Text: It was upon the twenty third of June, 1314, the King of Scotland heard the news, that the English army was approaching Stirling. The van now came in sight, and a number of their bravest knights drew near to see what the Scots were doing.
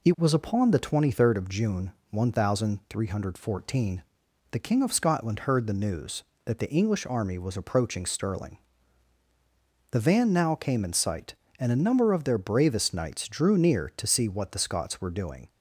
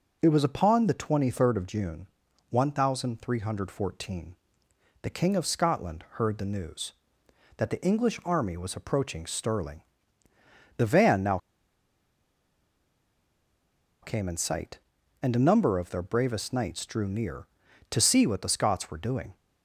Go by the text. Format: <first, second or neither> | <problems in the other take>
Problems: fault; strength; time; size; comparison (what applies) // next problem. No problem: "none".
first | pauses between "now" and "came"; strong; at 11.3 s; 2.6 s long